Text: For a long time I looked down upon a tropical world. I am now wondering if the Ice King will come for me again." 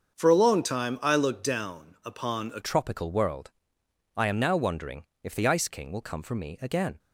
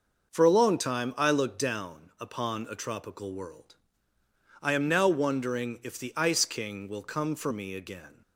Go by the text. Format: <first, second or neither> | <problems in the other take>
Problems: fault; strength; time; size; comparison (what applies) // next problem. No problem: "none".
second | starts louder than the rest; until 1.1 s; 7 dB // changes voice at "tropical"; from 2.6 s on; 4.3 s long // pauses between "wondering" and "if"; slight; at 5.0 s; 0.18 s long